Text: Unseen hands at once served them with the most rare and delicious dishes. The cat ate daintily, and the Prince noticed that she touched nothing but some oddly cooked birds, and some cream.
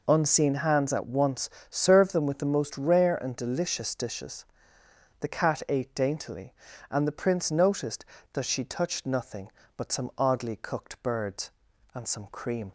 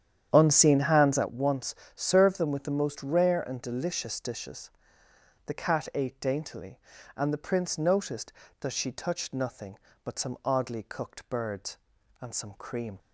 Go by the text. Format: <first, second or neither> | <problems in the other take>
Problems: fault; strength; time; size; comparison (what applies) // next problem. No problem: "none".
first | starts louder than the rest; strong; until 1.3 s; 9.5 dB // pauses between "once" and "served"; slight; at 1.7 s; 0.22 s long; slight in the first